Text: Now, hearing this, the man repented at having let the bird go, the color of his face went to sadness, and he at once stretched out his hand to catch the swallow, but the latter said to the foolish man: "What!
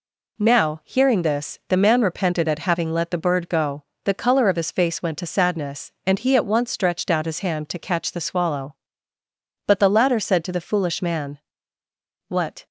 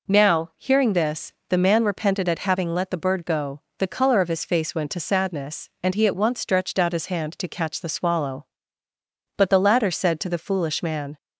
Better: first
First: none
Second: stops before "What"; at 11.1 s

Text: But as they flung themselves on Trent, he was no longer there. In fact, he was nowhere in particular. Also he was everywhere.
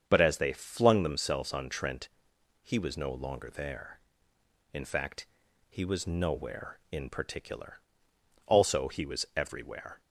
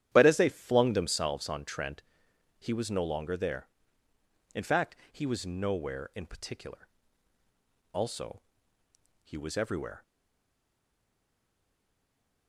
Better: first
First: starts louder than the rest; strong; until 1.0 s; 7.5 dB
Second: starts louder than the rest; strong; until 1.1 s; 10.5 dB // pauses between "Also" and "he"; noticeable; at 8.4 s; 0.82 s long // stays silent after the last word; from 10.0 s on; 2.4 s long

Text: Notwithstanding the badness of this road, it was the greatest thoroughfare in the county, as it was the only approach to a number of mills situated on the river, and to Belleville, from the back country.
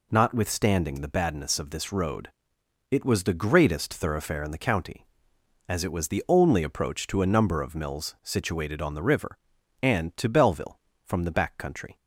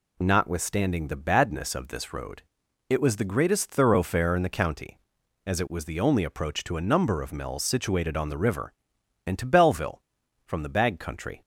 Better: first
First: none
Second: says "bag" for "back"; at 10.6 s

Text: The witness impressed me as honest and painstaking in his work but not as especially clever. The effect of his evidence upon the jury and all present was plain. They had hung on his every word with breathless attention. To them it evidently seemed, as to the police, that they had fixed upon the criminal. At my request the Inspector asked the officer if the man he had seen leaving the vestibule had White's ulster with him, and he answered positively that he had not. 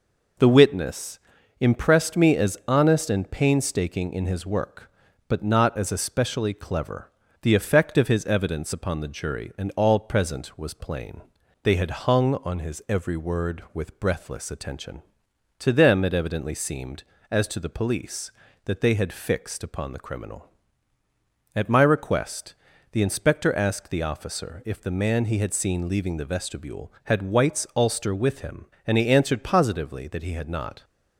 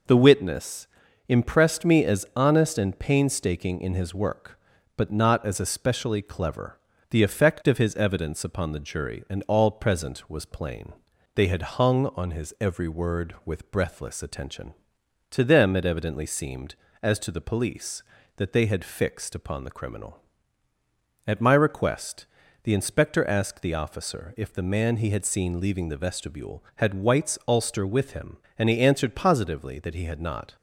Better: neither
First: pauses between "witness" and "impressed"; at 1.1 s; 0.42 s long // pauses between "request" and "the"; at 22.5 s; 0.38 s long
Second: pauses between "witness" and "impressed"; at 0.8 s; 0.42 s long // pauses between "request" and "the"; at 22.2 s; 0.38 s long

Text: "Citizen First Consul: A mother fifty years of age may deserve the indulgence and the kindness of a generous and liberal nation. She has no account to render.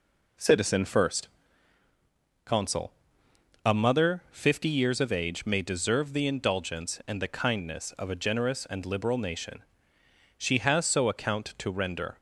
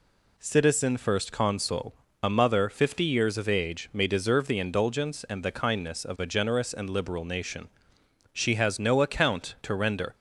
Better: second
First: pauses between "First" and "Consul"; at 1.2 s; 1.1 s long // says "so" for "no"; at 10.8 s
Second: none

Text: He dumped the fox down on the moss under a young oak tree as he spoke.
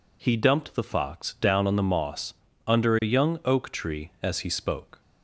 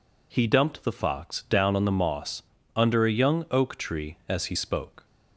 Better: neither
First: pauses between "moss" and "under"; slight; at 2.3 s; 0.34 s long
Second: pauses between "moss" and "under"; slight; at 2.4 s; 0.34 s long

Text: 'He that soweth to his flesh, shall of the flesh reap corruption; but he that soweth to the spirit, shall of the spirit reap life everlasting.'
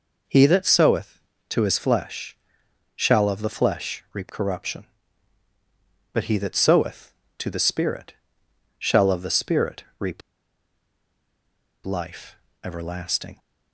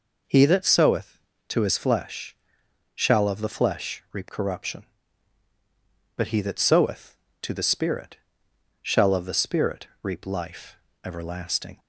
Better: second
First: pauses between "spirit" and "reap"; slight; at 9.8 s; 0.16 s long // pauses between "reap" and "life"; strong; at 10.2 s; 1.6 s long // pauses between "life" and "everlasting"; slight; at 12.3 s; 0.26 s long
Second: pauses between "spirit" and "reap"; slight; at 9.8 s; 0.16 s long // pauses between "life" and "everlasting"; slight; at 10.7 s; 0.26 s long

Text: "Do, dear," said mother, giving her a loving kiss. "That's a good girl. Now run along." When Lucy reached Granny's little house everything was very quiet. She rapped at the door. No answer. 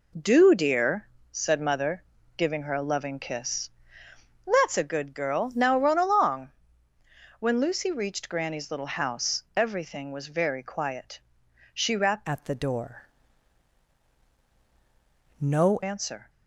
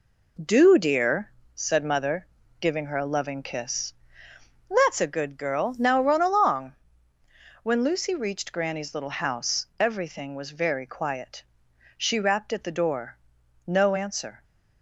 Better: second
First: pauses between "house" and "everything"; slight; at 9.4 s; 0.16 s long // changes voice from "at" to "No"; from 12.2 to 15.7 s; 3.5 s long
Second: pauses between "house" and "everything"; slight; at 9.6 s; 0.16 s long

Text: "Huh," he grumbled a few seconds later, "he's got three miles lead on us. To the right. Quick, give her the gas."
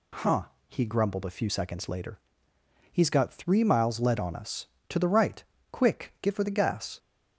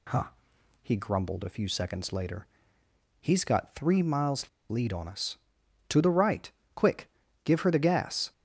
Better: first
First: none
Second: pauses between "miles" and "lead"; slight; at 4.4 s; 0.20 s long

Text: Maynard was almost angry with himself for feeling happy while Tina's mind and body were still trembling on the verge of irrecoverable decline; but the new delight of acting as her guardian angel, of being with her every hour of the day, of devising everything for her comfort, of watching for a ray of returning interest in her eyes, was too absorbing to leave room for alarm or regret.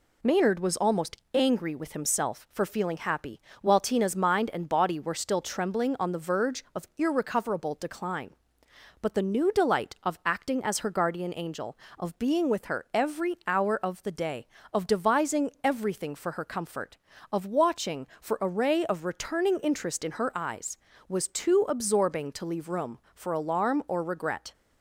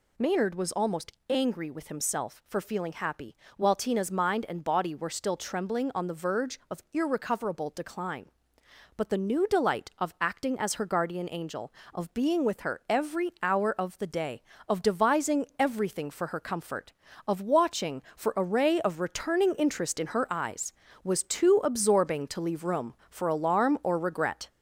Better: first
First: pauses between "almost" and "angry"; slight; at 1.1 s; 0.16 s long // pauses between "happy" and "while"; slight; at 3.4 s; 0.22 s long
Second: gets louder; throughout; 4 dB // pauses between "almost" and "angry"; slight; at 1.1 s; 0.16 s long // pauses between "happy" and "while"; slight; at 3.3 s; 0.22 s long

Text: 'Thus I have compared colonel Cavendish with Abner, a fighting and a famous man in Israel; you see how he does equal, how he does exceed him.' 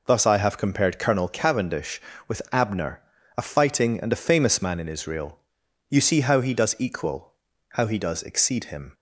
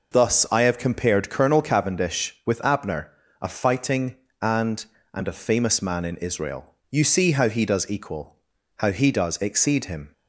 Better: first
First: none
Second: says "and" twice; at 5.1 s

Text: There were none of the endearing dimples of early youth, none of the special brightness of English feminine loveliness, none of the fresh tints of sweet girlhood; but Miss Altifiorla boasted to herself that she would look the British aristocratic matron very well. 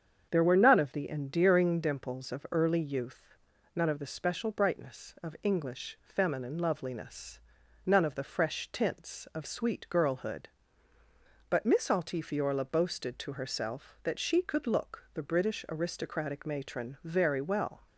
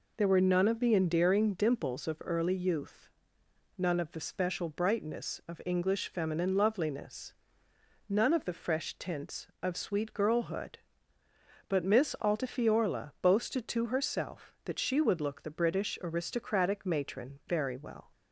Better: second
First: starts louder than the rest; strong; until 1.3 s; 7.5 dB // says "could" for "would"; at 14.4 s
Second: none

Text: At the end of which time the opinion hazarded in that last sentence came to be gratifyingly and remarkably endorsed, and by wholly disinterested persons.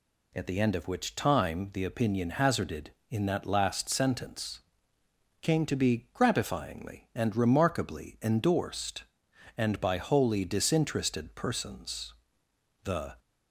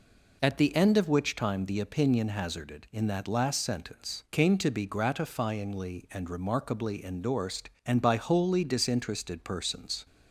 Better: second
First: pauses between "sentence" and "came"; noticeable; at 4.6 s; 0.82 s long // goes on to say "The"; slight; from 12.8 s on; 0.30 s long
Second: none

